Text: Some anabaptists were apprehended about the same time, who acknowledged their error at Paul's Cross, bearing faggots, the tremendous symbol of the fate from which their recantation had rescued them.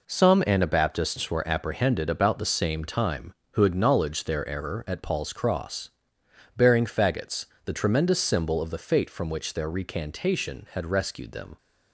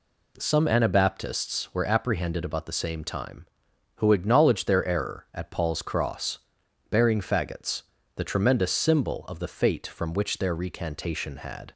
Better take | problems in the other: first | stops before "rescued them"; at 11.7 s

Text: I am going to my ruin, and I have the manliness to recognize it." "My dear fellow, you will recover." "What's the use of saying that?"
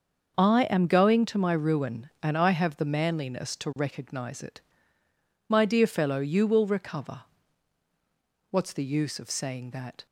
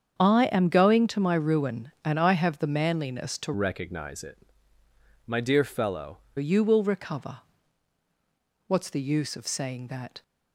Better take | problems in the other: first | starts louder than the rest; strong; until 1.2 s; 7.5 dB; also in the first // changes voice from "recognize" to "fellow"; from 3.5 to 6.1 s; 2.6 s long

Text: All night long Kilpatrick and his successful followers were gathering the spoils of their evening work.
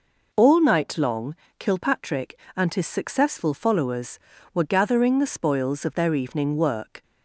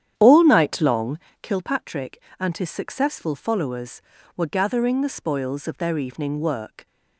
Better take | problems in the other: first | starts louder than the rest; strong; until 1.5 s; 10 dB // pauses between "long" and "Kilpatrick"; slight; at 1.1 s; 0.22 s long; slight in the first

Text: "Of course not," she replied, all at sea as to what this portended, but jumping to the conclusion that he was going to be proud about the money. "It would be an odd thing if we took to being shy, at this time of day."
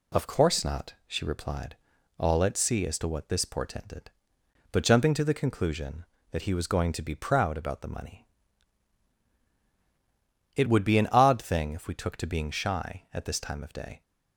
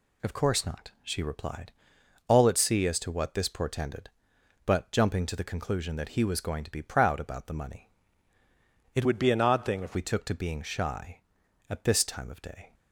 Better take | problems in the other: first | changes voice from "would" to "if"; from 9.0 to 9.9 s; 0.9 s long

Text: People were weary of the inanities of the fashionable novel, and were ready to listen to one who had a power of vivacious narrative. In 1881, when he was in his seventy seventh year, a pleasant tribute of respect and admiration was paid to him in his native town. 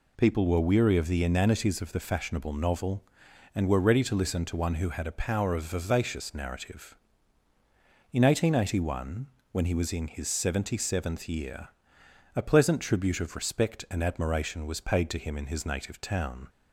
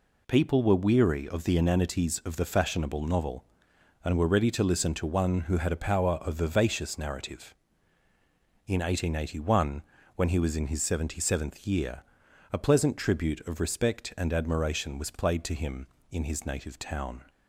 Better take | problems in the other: first | says "played" for "paid"; at 15.1 s

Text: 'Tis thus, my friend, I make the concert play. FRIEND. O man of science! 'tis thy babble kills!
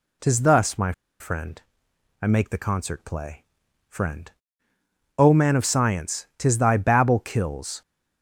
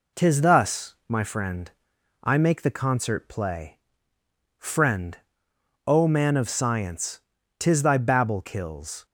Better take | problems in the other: second | pauses between "my" and "friend"; slight; at 0.9 s; 0.28 s long

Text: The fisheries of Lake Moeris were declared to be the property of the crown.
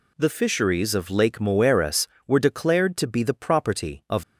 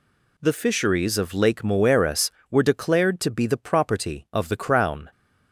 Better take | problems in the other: second | stops before "the crown"; at 4.2 s

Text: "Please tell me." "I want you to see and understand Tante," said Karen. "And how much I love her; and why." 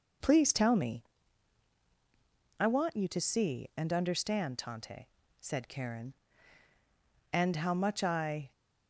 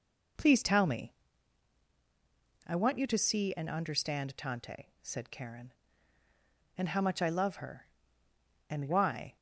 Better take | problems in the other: second | stops before "love her and why"; at 8.5 s

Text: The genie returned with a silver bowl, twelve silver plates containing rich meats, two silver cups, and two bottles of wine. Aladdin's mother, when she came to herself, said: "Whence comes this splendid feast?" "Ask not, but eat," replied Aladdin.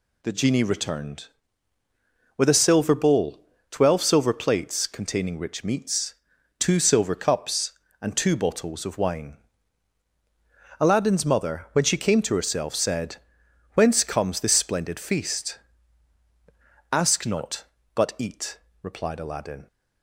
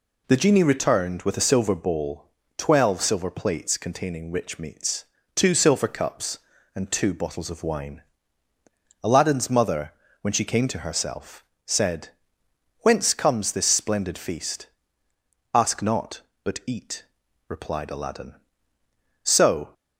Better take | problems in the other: first | goes on to say "So"; from 19.2 s on; 0.50 s long

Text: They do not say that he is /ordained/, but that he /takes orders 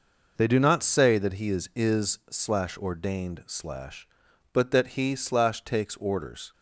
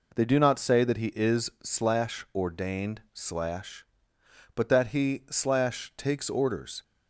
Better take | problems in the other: second | says "is" twice; at 1.7 s

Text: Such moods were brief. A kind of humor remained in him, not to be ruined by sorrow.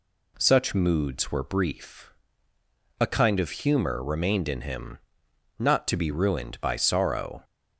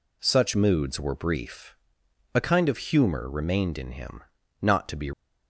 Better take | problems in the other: first | stops before "ruined by sorrow"; at 5.1 s

